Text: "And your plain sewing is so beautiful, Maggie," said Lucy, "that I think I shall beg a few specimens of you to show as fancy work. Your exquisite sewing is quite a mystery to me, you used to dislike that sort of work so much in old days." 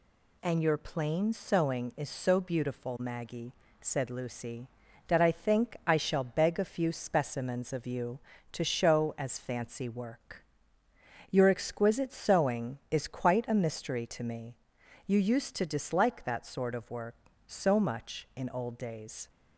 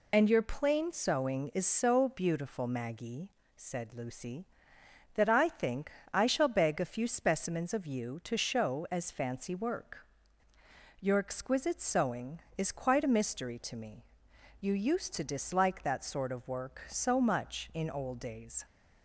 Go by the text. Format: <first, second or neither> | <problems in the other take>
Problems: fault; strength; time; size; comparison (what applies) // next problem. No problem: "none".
first | loses the start of "And"; at 0.1 s; 20 ms // pauses between "think" and "I"; slight; at 5.9 s; 0.20 s long